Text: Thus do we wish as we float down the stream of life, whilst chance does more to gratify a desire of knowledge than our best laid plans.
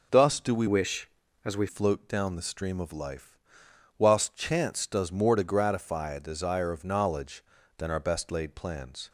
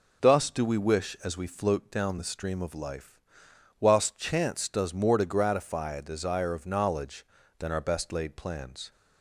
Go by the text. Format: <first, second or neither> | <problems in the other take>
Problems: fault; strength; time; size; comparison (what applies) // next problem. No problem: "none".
second | changes voice from "wish" to "we"; from 0.6 to 1.6 s; 1.0 s long